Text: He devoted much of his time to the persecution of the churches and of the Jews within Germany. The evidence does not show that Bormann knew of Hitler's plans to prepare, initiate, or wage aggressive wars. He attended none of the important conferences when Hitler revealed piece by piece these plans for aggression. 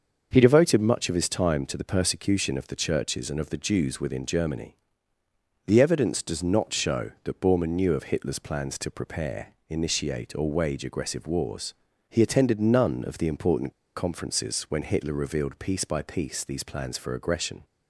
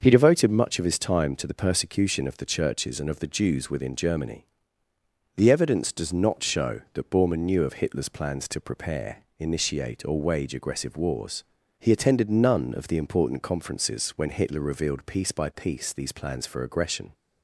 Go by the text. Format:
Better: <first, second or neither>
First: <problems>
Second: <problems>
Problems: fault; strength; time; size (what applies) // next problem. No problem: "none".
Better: second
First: starts louder than the rest; until 1.3 s; 6.5 dB // pauses between "important" and "conferences"; slight; at 13.7 s; 0.23 s long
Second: starts louder than the rest; until 1.0 s; 6.5 dB